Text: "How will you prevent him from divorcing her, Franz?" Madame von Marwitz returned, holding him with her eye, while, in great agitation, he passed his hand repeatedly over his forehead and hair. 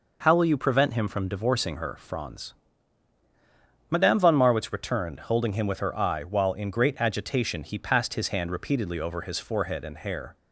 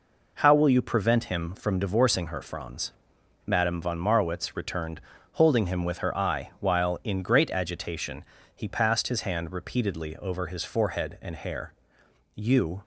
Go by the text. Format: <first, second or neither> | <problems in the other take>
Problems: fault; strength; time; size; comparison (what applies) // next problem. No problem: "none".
first | goes on to say "You"; slight; from 12.3 s on; 0.48 s long